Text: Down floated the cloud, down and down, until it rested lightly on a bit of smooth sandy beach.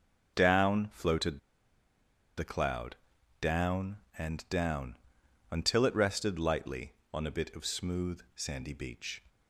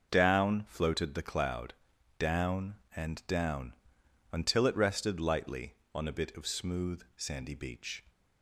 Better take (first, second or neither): second